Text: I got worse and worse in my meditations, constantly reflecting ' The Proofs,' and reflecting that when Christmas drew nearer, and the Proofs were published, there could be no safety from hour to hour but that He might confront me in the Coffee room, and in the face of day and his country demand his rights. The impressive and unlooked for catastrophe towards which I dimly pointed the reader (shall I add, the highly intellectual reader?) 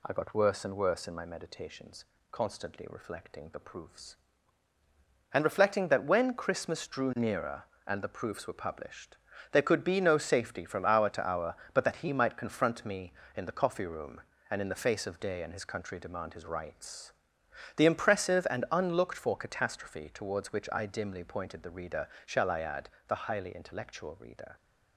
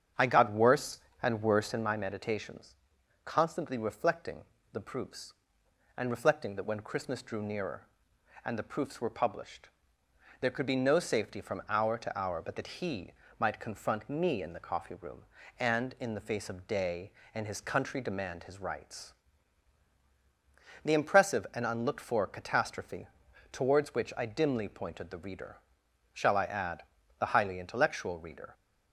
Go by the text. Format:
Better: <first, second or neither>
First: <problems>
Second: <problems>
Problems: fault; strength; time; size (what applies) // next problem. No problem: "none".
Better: first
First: none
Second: starts louder than the rest; strong; until 1.9 s; 8 dB // pauses between "He" and "might"; slight; at 13.1 s; 0.28 s long // pauses between "catastrophe" and "towards"; at 23.0 s; 0.42 s long